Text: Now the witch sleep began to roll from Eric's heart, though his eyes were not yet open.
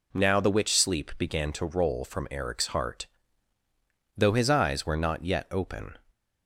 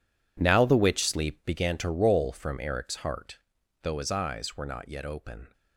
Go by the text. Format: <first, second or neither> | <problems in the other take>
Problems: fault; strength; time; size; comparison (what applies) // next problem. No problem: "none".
first | gets quieter; strong; throughout; 13 dB